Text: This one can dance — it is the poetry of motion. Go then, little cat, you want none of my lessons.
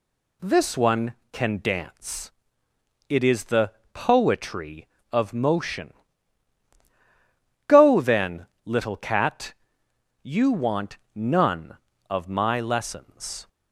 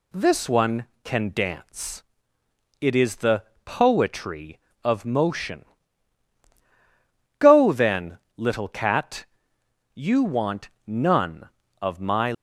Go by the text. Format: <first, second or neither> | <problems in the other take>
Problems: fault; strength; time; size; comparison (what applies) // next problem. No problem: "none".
first | pauses between "the" and "poetry"; slight; at 3.4 s; 0.20 s long; slight in the first // pauses between "want" and "none"; slight; at 10.6 s; 0.18 s long; slight in the first // stops before "lessons"; at 12.3 s